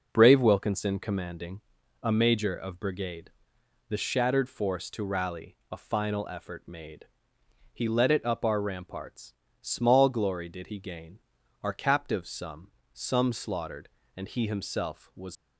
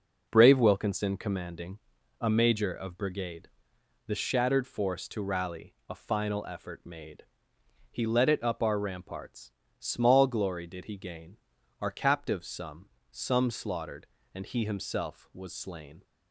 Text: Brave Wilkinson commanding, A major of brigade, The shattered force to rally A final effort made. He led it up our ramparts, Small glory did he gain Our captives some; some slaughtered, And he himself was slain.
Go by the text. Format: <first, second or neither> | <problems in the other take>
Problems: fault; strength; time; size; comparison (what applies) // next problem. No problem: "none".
second | pauses between "rally" and "A"; slight; at 5.5 s; 0.16 s long; slight in the second // pauses between "gain" and "Our"; at 11.1 s; 0.42 s long; also in the second // stops before "slain"; at 15.3 s